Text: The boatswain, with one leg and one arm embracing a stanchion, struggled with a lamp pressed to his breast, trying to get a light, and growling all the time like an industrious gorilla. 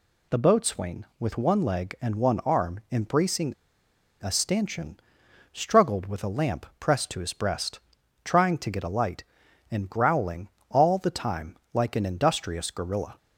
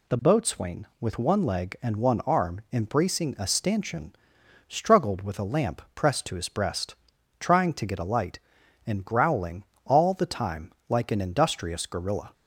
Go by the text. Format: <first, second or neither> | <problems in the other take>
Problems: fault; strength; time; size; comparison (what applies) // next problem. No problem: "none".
second | pauses between "embracing" and "a"; noticeable; at 3.5 s; 0.67 s long // pauses between "growling" and "all"; slight; at 10.4 s; 0.20 s long; slight in the second // pauses between "time" and "like"; slight; at 11.5 s; 0.16 s long; slight in the second